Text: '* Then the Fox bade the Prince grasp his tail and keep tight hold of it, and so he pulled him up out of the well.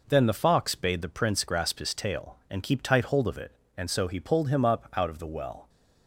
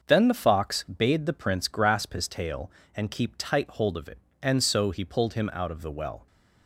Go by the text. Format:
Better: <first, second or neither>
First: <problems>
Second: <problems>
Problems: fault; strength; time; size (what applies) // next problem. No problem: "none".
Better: first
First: none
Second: starts louder than the rest; noticeable; until 1.0 s; 6 dB // skips "up"; at 5.5 s